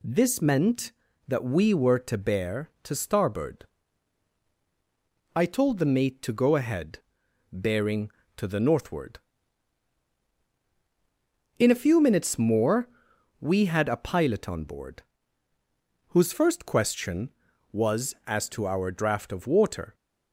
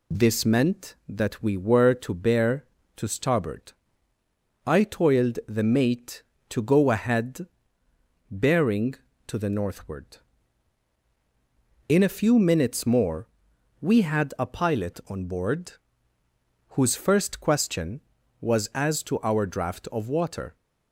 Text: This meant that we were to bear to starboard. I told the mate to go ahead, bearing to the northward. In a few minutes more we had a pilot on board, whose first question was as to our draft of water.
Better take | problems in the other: first | says "toiled" for "told"; at 4.8 s // pauses between "more" and "we"; noticeable; at 13.2 s; 0.54 s long; noticeable in the first

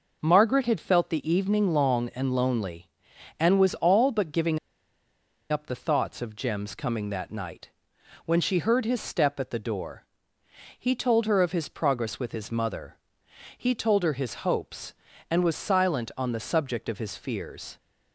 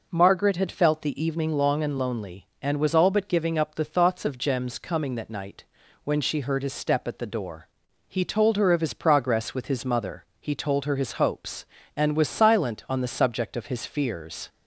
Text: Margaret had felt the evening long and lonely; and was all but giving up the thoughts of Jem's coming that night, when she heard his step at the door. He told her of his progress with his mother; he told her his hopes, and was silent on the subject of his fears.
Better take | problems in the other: second | pauses between "giving" and "up"; noticeable; at 4.5 s; 0.92 s long

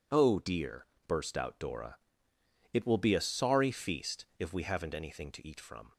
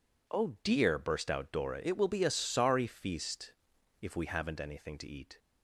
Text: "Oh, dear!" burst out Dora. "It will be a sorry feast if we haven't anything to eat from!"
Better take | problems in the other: first | pauses between "feast" and "if"; noticeable; at 3.5 s; 0.48 s long // stops before "from"; at 5.3 s

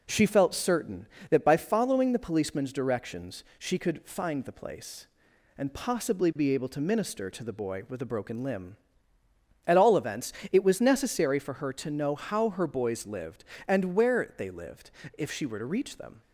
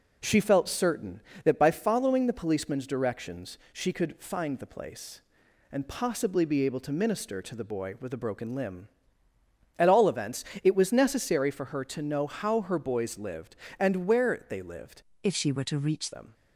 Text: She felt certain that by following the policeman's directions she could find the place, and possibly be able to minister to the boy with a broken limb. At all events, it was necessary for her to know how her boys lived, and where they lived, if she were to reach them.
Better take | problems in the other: first | pauses between "directions" and "she"; slight; at 3.5 s; 0.16 s long; slight in the first // changes voice from "if" to "reach"; from 15.2 to 16.1 s; 0.9 s long

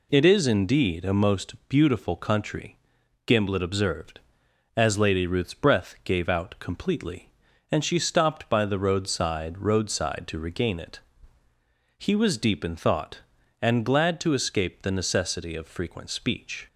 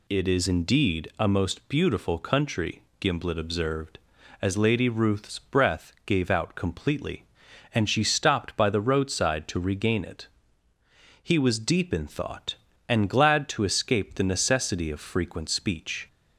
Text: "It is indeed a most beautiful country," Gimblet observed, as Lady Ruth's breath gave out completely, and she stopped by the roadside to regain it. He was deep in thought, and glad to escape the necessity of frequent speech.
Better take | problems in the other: second | says "roadside" twice; at 9.5 s

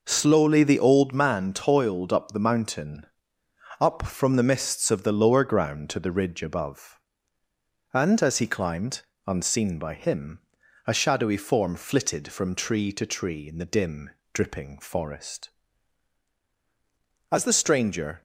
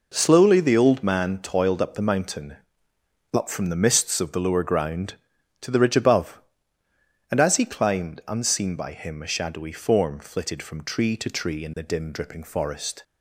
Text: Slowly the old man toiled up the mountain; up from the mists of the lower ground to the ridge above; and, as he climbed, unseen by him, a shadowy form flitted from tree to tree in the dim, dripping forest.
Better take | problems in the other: second | goes on to say "As the stranger"; noticeable; from 17.2 s on; 0.92 s long

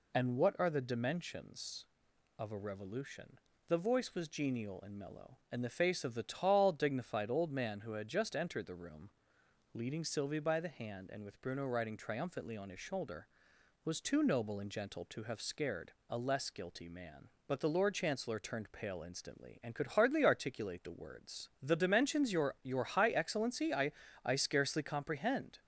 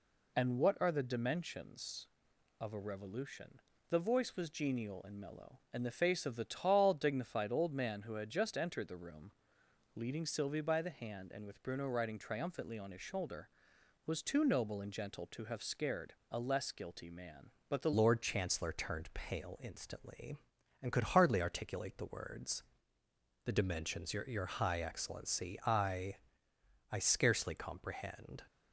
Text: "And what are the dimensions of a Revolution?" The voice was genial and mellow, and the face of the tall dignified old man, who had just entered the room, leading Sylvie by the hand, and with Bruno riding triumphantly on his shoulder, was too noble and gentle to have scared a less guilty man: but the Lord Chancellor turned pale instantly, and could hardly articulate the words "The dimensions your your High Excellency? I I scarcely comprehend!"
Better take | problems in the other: first | pauses between "scared" and "a"; slight; at 16.1 s; 0.16 s long; slight in the first // changes voice at "Lord"; from 17.9 s on; 10.5 s long // pauses between "words" and "The"; noticeable; at 22.6 s; 0.84 s long // pauses between "I" and "I"; noticeable; at 26.1 s; 0.74 s long; slight in the first

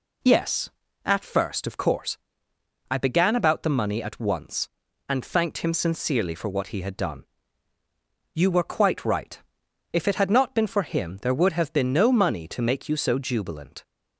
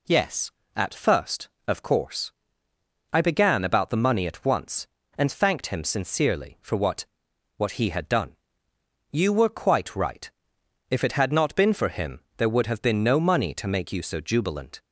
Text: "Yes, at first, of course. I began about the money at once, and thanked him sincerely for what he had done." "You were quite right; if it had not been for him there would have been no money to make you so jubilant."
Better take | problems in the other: first | says "what" twice; at 7.5 s // pauses between "him" and "there"; slight; at 12.2 s; 0.17 s long

